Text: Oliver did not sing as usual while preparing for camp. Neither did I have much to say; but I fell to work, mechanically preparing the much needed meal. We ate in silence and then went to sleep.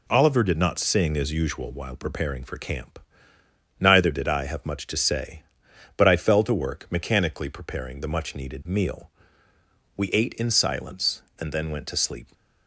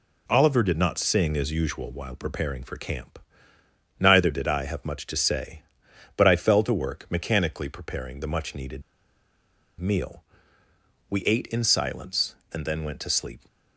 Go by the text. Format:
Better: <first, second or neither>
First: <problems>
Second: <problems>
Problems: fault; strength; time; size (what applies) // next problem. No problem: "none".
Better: first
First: none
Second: pauses between "needed" and "meal"; at 8.8 s; 0.98 s long